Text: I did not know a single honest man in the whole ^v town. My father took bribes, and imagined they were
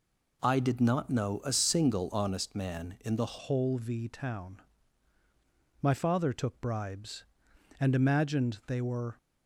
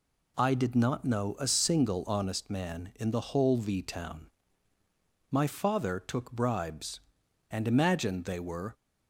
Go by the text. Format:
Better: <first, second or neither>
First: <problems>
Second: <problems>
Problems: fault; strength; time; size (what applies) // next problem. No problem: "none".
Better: second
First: changes voice at "whole"; from 3.3 s on; 5.8 s long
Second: none